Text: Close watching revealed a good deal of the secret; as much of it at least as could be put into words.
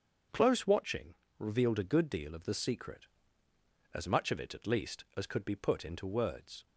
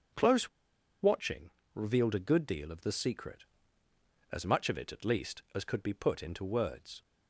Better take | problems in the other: first | starts louder than the rest; until 1.9 s; 7 dB; also in the first // pauses between "Close" and "watching"; noticeable; at 0.4 s; 0.53 s long // pauses between "watching" and "revealed"; slight; at 1.5 s; 0.24 s long; slight in the first

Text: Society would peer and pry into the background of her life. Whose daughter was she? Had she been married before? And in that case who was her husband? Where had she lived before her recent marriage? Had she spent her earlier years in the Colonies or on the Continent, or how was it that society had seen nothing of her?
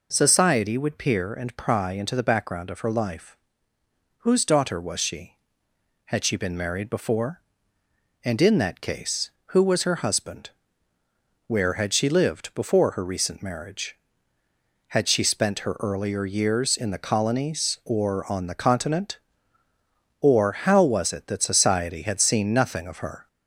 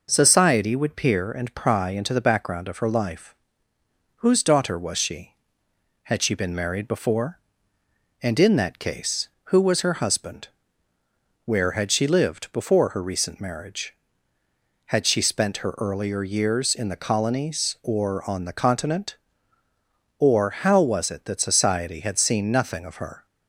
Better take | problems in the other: second | gets louder; slight; throughout; 2.5 dB

